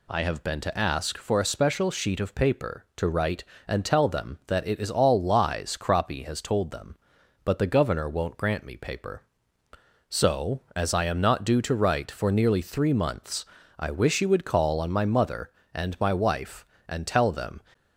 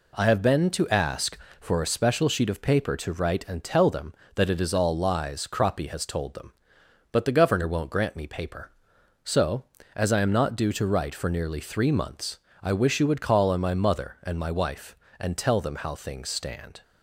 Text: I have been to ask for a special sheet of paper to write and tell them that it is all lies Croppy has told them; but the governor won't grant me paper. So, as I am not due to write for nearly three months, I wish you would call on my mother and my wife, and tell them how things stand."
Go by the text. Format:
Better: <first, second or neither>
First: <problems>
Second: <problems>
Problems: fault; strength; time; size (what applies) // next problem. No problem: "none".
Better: second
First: stops before "how things stand"; at 17.7 s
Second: none